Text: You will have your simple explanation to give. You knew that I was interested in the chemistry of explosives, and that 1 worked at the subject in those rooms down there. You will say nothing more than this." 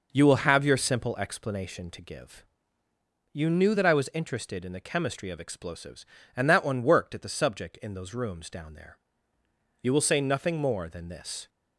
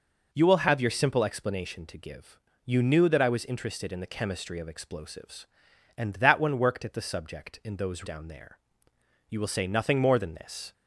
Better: first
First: none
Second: skips "rooms"; at 8.0 s

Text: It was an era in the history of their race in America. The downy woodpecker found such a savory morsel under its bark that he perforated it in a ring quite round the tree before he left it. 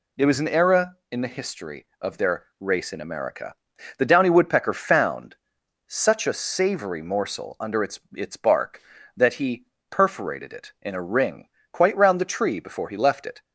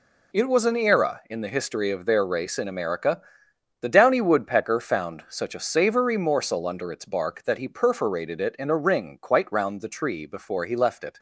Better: second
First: pauses between "their" and "race"; slight; at 2.4 s; 0.16 s long // pauses between "found" and "such"; noticeable; at 5.3 s; 0.54 s long // says "its" twice; at 8.1 s // pauses between "he" and "perforated"; slight; at 9.6 s; 0.24 s long // pauses between "ring" and "quite"; slight; at 11.4 s; 0.24 s long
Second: none

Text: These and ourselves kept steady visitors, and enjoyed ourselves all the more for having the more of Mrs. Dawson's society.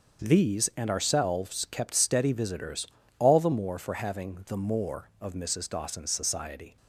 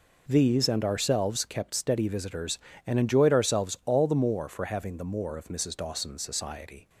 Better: second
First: starts louder than the rest; until 1.2 s; 6.5 dB // skips "and enjoyed ourselves"; at 3.0 s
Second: none

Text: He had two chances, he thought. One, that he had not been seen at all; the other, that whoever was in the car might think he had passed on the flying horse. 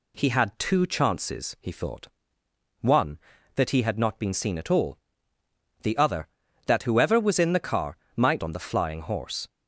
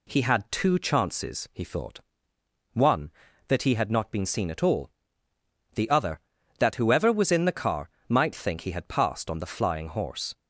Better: second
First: pauses between "car" and "might"; slight; at 7.9 s; 0.18 s long // skips "think he had passed"; at 8.4 s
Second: pauses between "car" and "might"; slight; at 7.8 s; 0.18 s long

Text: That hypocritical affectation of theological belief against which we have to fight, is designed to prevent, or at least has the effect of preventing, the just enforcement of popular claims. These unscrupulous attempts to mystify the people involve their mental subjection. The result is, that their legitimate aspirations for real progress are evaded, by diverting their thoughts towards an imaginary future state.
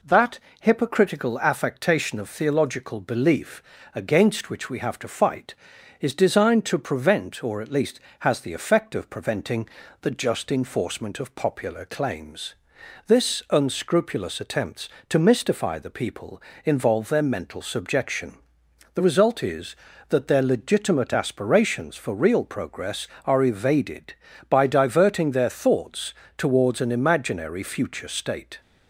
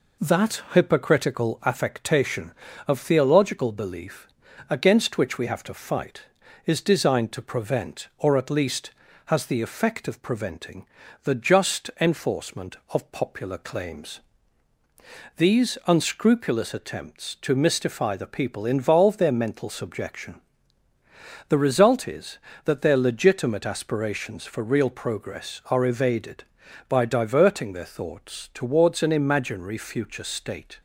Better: second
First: pauses between "That" and "hypocritical"; slight; at 0.3 s; 0.22 s long // pauses between "belief" and "against"; slight; at 3.6 s; 0.32 s long // says "This" for "These"; at 13.0 s // pauses between "people" and "involve"; slight; at 16.4 s; 0.24 s long // pauses between "thoughts" and "towards"; slight; at 26.1 s; 0.24 s long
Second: pauses between "belief" and "against"; at 4.2 s; 0.42 s long

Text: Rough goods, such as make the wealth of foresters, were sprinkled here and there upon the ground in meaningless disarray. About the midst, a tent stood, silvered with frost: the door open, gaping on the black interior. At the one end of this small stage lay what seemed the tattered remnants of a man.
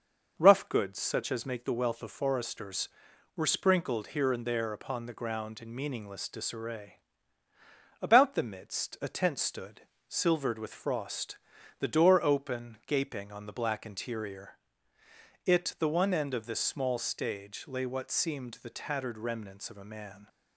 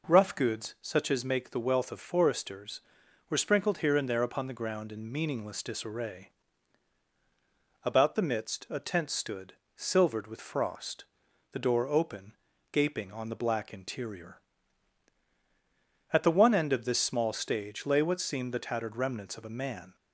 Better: second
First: starts louder than the rest; noticeable; until 1.3 s; 6 dB // says "It" for "At"; at 15.4 s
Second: none

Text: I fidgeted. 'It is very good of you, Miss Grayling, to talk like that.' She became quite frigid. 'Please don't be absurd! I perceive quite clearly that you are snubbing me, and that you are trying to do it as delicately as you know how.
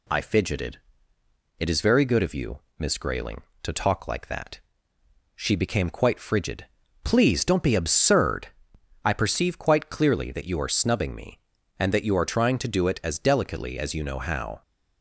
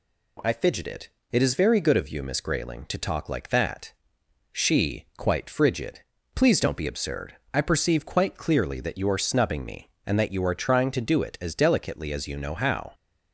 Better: first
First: none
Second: skips "became"; at 5.1 s

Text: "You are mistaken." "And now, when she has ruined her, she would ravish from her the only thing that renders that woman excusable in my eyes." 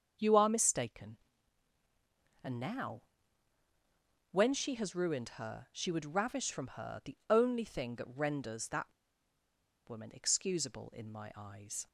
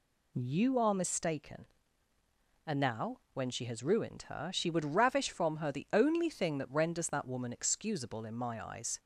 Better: second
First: starts louder than the rest; until 2.4 s; 7 dB // pauses between "that" and "woman"; at 8.9 s; 0.98 s long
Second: none

